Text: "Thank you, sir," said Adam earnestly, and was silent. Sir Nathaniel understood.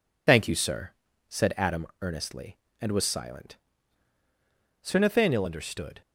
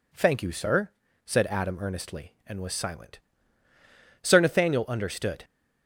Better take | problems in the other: second | loses the start of "Thank"; at 0.2 s; 35 ms

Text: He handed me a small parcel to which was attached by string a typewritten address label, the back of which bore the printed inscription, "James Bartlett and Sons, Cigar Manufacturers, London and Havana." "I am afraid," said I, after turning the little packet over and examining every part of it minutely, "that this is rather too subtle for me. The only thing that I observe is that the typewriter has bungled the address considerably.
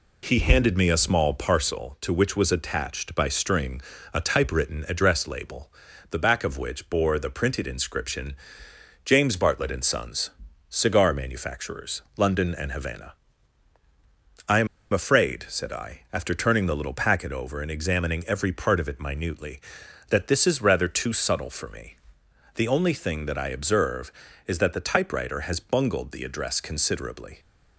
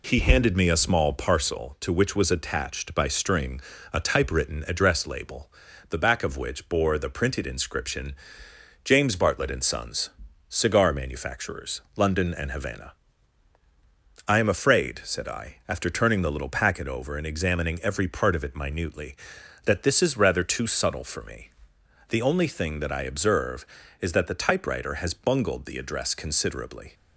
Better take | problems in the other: second | pauses between "string" and "a"; slight; at 3.8 s; 0.32 s long; slight in the second // pauses between "am" and "afraid"; slight; at 14.6 s; 0.26 s long

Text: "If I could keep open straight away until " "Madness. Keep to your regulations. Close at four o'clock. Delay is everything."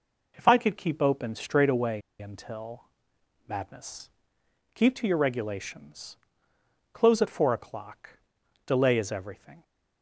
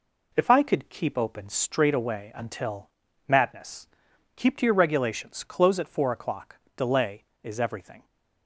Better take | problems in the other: second | pauses between "away" and "until"; slight; at 2.0 s; 0.19 s long

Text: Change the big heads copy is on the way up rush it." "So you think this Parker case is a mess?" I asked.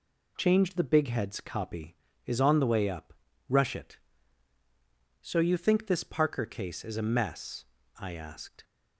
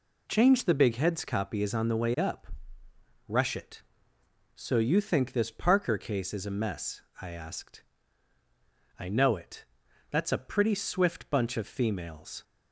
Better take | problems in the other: first | pauses between "up" and "rush"; noticeable; at 2.4 s; 0.80 s long; also in the first // goes on to say "I know it That's a pretty swift bunch of females"; strong; from 8.9 s on; 3.4 s long

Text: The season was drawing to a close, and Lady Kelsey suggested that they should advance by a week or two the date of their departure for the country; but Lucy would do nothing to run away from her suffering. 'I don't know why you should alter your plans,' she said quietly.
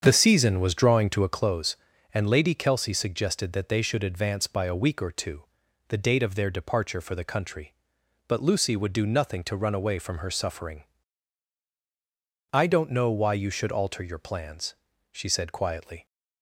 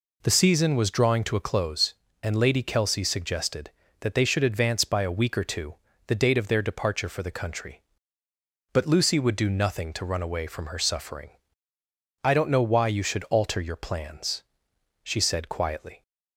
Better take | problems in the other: second | starts louder than the rest; strong; until 1.3 s; 7.5 dB // pauses between "two" and "the"; at 5.4 s; 0.42 s long; slight in the second

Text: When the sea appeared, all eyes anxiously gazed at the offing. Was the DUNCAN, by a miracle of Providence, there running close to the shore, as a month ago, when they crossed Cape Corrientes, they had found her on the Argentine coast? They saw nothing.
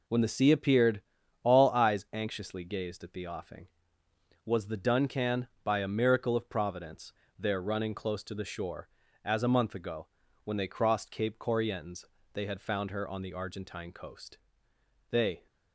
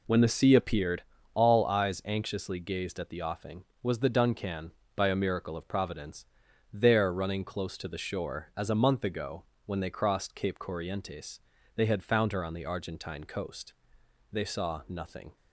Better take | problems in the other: second | stops before "saw nothing"; at 15.4 s

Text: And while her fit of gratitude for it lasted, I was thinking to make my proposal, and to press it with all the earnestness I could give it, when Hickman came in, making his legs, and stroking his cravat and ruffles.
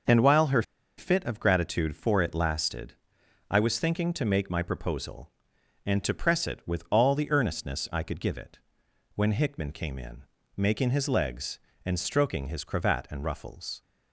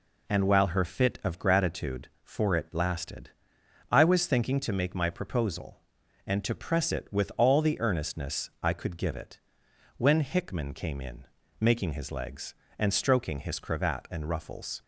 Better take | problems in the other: second | pauses between "her" and "fit"; slight; at 0.6 s; 0.35 s long

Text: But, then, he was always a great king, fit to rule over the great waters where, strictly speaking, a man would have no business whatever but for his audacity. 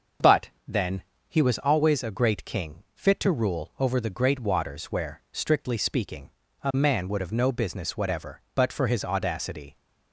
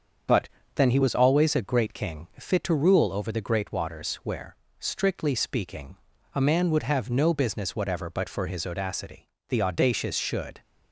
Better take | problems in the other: first | starts louder than the rest; until 1.5 s; 7 dB // goes on to say "The audacious should"; noticeable; from 9.4 s on; 1.1 s long

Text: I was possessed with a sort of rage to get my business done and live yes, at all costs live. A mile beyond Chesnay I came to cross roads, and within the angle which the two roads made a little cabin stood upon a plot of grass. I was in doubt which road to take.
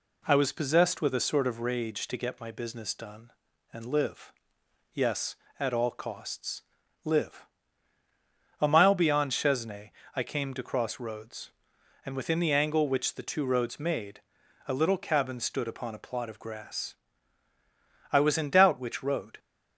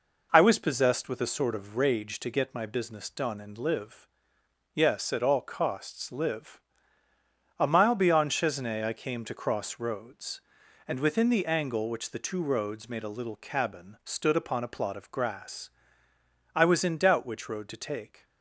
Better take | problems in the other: second | pauses between "live" and "yes"; noticeable; at 4.3 s; 0.62 s long; noticeable in the second // pauses between "costs" and "live"; at 6.6 s; 0.40 s long // pauses between "Chesnay" and "I"; slight; at 9.9 s; 0.24 s long // pauses between "made" and "a"; noticeable; at 14.2 s; 0.48 s long // stops before "to take"; at 19.3 s

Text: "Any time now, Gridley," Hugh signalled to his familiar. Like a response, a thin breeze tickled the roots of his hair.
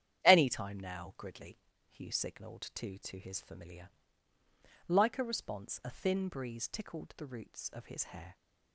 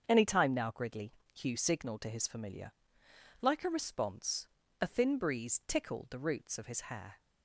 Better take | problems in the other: second | starts louder than the rest; strong; until 1.2 s; 9.5 dB; also in the second // says "to" twice; at 2.9 s

